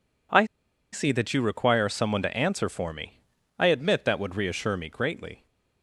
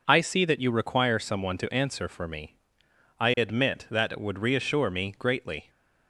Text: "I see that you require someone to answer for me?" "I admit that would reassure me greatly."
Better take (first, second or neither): second